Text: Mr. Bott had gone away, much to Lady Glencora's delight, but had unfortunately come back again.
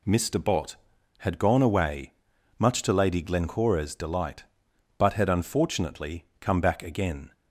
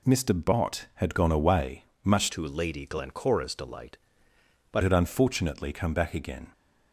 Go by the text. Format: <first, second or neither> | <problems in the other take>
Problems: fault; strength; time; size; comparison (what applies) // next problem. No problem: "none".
first | changes voice from "to" to "but"; from 2.3 to 4.8 s; 2.5 s long